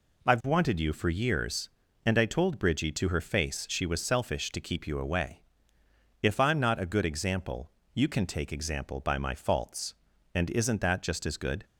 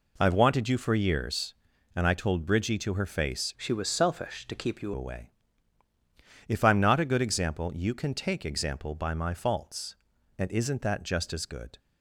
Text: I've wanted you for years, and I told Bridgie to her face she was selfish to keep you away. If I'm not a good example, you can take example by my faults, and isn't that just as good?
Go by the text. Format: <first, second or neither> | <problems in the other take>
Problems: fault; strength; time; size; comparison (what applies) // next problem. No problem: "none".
first | changes voice from "she" to "you"; from 3.5 to 4.9 s; 1.4 s long